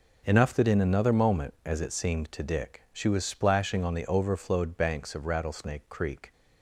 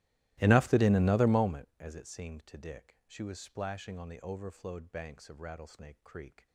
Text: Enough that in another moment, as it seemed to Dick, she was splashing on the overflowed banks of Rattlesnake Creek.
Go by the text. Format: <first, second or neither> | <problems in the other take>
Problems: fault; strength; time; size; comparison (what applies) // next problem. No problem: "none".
first | starts louder than the rest; strong; until 1.7 s; 17.5 dB